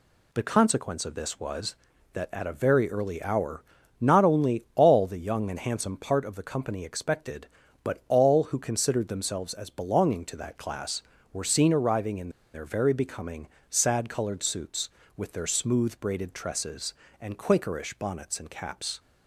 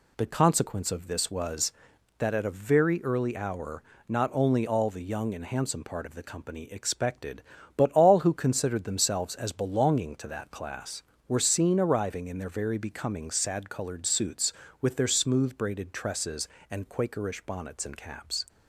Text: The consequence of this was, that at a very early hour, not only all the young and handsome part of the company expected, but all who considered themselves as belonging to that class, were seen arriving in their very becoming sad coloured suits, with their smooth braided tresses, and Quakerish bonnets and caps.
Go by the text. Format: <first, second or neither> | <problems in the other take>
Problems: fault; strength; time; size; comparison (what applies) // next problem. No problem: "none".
second | pauses between "in" and "their"; slight; at 12.2 s; 0.24 s long // pauses between "becoming" and "sad"; slight; at 13.4 s; 0.24 s long